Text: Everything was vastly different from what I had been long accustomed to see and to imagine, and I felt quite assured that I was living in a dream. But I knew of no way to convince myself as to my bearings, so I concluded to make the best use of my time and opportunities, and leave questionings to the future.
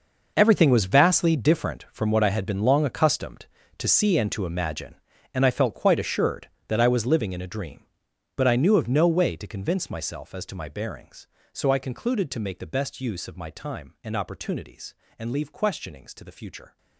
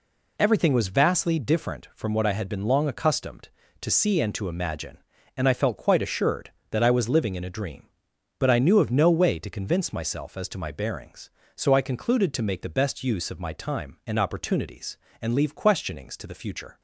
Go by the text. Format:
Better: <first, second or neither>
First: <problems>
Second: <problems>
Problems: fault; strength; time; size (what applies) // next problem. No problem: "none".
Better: second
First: gets quieter; strong; throughout; 15 dB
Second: none